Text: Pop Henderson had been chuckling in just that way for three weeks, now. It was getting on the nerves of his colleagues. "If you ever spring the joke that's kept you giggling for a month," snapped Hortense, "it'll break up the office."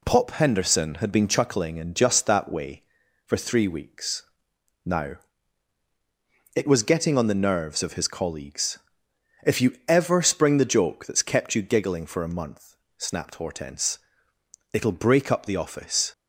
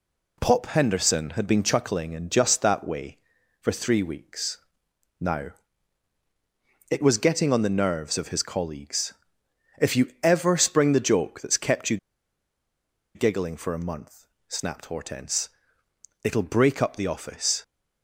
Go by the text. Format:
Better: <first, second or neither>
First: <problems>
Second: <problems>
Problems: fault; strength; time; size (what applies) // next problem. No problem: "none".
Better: first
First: none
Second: pauses between "you" and "giggling"; at 11.9 s; 1.1 s long